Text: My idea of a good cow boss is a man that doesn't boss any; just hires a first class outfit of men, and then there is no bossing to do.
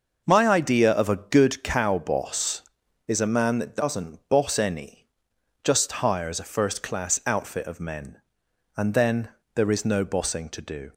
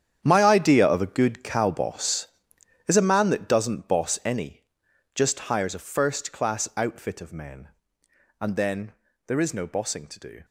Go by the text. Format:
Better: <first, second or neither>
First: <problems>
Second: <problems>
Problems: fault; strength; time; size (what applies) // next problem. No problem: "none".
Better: first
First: pauses between "then" and "there"; slight; at 9.2 s; 0.28 s long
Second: gets quieter; strong; throughout; 14.5 dB // pauses between "then" and "there"; slight; at 8.9 s; 0.36 s long